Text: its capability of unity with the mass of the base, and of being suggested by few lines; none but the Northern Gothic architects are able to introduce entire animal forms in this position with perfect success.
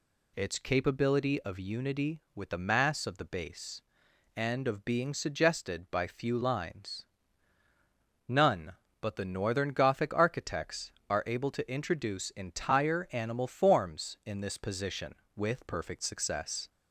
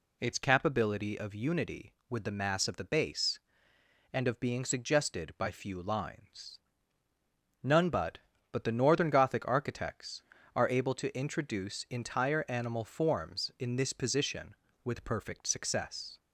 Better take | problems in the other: first | says "but" twice; at 8.5 s

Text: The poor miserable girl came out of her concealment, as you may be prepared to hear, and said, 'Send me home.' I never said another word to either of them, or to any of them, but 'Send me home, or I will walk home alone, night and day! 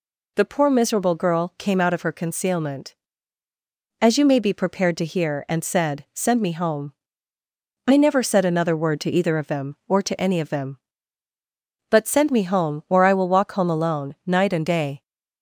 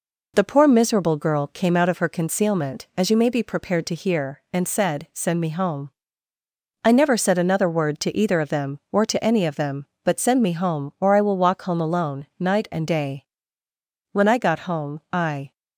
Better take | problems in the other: first | goes on to say "When I got home I"; from 14.1 s on; 1.4 s long

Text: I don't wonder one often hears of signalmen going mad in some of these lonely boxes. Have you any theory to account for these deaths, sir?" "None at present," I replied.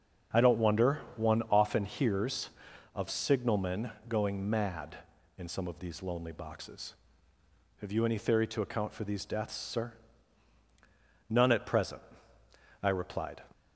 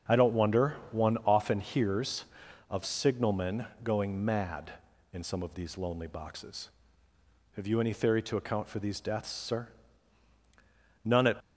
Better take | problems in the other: first | starts louder than the rest; strong; until 1.3 s; 8 dB; strong in the first // pauses between "wonder" and "one"; slight; at 0.7 s; 0.18 s long; slight in the first // pauses between "signalmen" and "going"; slight; at 3.6 s; 0.18 s long; slight in the first // stops before "present I replied"; at 11.4 s

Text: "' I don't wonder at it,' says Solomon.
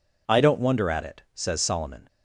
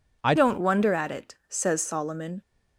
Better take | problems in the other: first | changes voice at "don't"; from 0.3 s on; 2.1 s long

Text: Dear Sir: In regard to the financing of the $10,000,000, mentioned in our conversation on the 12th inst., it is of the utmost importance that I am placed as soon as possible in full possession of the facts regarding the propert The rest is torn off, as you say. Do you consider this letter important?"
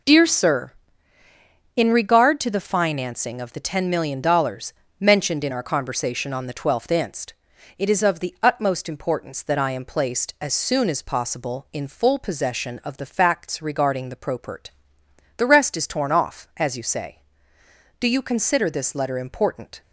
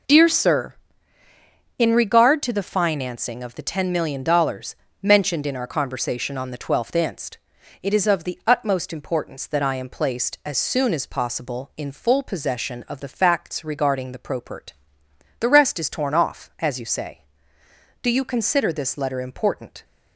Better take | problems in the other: neither | pauses between "propert" and "The"; noticeable; the same in both

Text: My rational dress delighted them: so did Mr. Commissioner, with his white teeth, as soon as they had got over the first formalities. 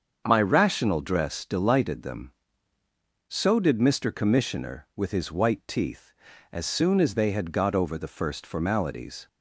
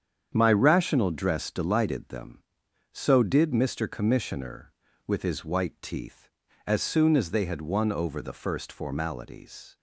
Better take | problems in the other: first | starts louder than the rest; strong; until 1.3 s; 8 dB; also in the first // says "won" for "got"; at 7.6 s

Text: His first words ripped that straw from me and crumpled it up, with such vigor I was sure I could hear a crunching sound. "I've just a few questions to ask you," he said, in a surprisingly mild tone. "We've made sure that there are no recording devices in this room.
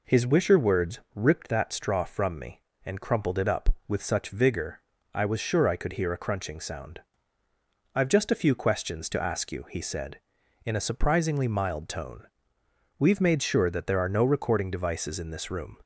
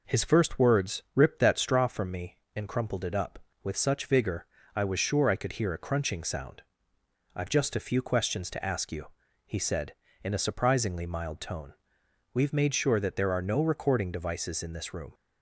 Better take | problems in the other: second | says "wisher" for "first"; at 0.2 s // pauses between "words" and "ripped"; slight; at 0.9 s; 0.16 s long // pauses between "vigor" and "I"; slight; at 4.7 s; 0.36 s long; slight in the second

